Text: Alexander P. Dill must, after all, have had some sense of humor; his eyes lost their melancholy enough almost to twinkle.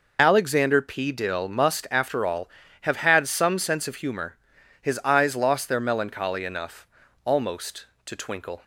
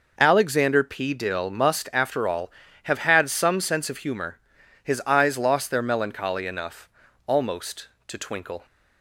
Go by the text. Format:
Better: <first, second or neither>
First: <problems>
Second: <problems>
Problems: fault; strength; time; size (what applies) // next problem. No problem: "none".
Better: second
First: loses the start of "Alexander"; at 0.1 s; 30 ms // pauses between "enough" and "almost"; at 6.8 s; 0.38 s long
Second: pauses between "enough" and "almost"; at 6.8 s; 0.38 s long